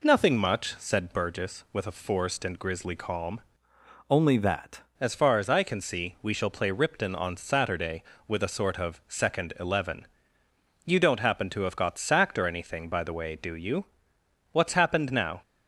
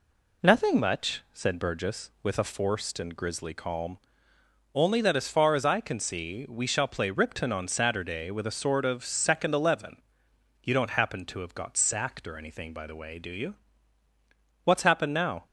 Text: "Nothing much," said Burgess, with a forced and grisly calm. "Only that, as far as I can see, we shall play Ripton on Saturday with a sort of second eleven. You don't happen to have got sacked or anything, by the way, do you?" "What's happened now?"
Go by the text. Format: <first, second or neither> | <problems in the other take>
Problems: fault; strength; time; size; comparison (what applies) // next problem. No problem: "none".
second | changes voice from "Only" to "that"; from 4.0 to 4.8 s; 0.8 s long